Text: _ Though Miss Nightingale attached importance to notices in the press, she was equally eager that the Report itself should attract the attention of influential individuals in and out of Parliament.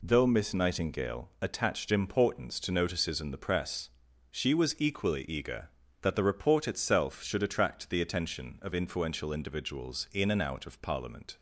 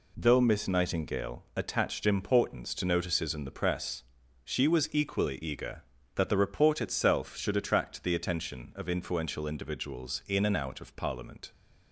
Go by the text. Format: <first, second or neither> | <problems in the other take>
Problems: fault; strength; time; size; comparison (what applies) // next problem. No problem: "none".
neither | none